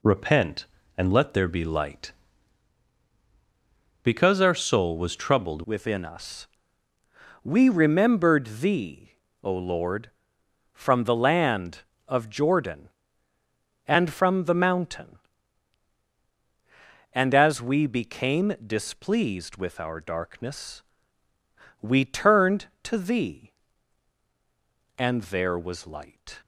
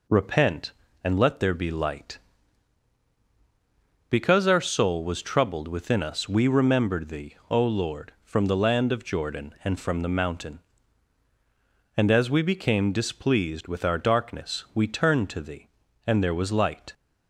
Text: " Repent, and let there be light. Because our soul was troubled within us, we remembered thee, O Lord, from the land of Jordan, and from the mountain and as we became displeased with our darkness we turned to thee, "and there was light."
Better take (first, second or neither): second